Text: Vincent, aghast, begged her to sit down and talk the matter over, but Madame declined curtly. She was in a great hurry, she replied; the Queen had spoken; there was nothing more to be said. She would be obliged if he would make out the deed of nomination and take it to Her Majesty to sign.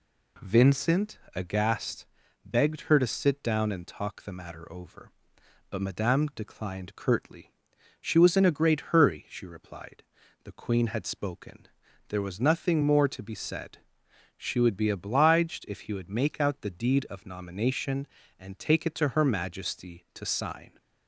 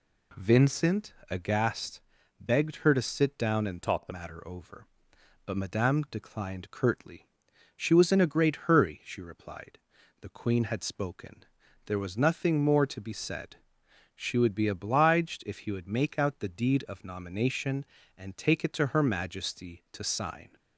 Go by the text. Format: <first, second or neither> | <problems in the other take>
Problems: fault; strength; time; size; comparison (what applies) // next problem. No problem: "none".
first | changes voice from "talk" to "the"; from 3.8 to 4.1 s; 0.3 s long